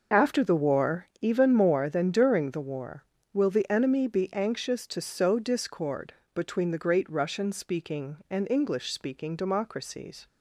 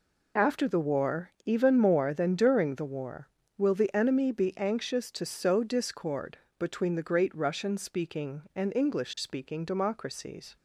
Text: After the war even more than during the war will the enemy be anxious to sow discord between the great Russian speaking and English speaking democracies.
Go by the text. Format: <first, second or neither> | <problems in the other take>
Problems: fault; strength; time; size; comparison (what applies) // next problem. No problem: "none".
second | starts louder than the rest; noticeable; until 1.3 s; 5.5 dB // pauses between "war" and "even"; slight; at 1.0 s; 0.16 s long; slight in the second // pauses between "discord" and "between"; slight; at 6.1 s; 0.22 s long; slight in the second